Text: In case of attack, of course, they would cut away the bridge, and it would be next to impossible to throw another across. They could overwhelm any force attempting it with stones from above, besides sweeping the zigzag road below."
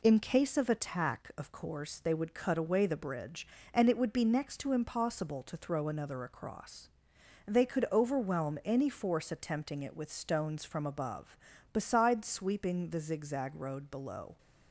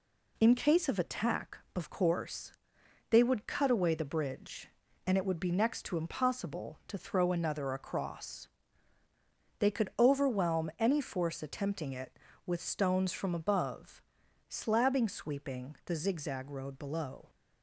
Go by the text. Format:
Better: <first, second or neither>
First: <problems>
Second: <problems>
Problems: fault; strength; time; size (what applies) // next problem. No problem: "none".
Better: first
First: none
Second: says "slabbing" for "besides"; at 14.4 s